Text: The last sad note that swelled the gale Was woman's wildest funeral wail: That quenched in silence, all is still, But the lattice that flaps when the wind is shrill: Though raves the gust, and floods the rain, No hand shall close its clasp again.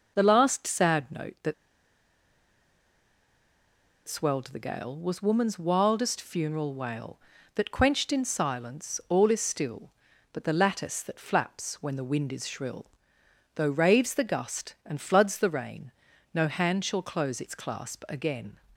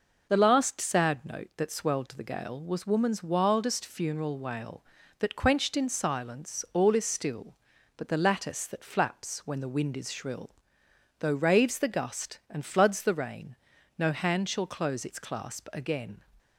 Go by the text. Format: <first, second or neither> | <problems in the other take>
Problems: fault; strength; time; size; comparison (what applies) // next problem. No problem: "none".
second | pauses between "that" and "swelled"; strong; at 1.5 s; 2.5 s long